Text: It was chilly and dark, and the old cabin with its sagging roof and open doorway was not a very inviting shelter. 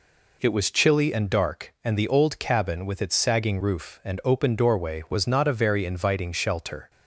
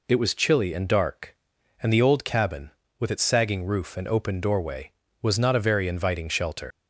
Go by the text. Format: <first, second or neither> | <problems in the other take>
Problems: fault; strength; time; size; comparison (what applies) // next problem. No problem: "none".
first | leaves "shelter" unfinished; at 6.7 s; 95 ms